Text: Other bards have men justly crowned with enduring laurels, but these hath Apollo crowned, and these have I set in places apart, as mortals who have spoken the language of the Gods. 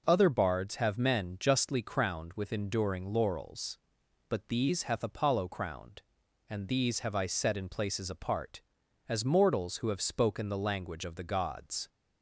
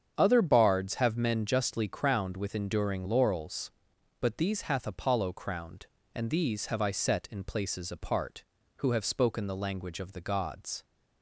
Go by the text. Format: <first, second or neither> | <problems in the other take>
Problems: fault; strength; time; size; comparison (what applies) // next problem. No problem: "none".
first | starts louder than the rest; strong; until 1.2 s; 7.5 dB // skips "as mortals"; at 8.6 s